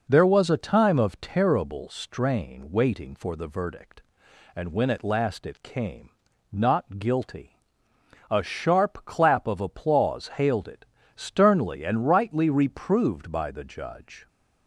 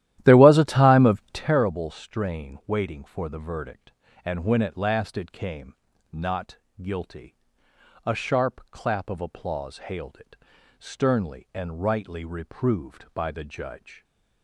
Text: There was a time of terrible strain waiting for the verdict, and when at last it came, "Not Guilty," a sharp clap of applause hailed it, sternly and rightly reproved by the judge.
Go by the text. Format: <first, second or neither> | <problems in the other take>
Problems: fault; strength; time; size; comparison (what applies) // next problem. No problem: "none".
first | starts louder than the rest; strong; until 1.6 s; 13 dB // pauses between "Not" and "Guilty"; slight; at 6.5 s; 0.24 s long